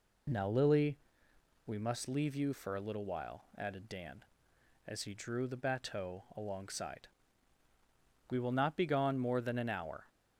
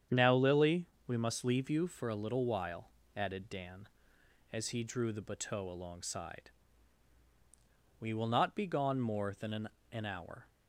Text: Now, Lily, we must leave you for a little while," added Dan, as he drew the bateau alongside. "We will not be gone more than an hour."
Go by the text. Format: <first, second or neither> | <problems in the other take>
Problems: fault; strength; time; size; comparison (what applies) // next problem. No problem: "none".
first | starts louder than the rest; strong; until 1.3 s; 8.5 dB // says "an" twice; at 9.9 s